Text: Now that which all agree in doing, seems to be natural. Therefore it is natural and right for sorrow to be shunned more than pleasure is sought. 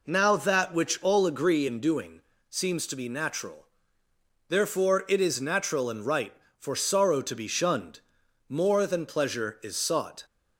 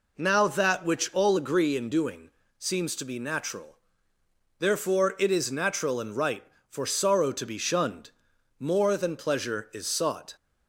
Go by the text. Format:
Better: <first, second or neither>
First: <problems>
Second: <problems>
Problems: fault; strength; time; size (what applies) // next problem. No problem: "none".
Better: neither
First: pauses between "shunned" and "more"; noticeable; at 7.9 s; 0.50 s long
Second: pauses between "shunned" and "more"; noticeable; at 8.0 s; 0.50 s long